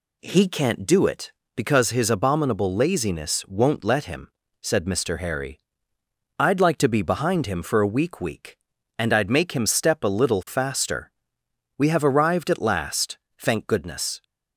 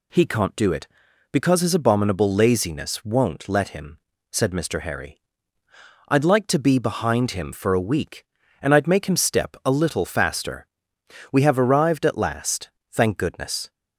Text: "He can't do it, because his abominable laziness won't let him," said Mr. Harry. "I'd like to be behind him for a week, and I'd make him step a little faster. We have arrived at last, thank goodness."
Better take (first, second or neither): second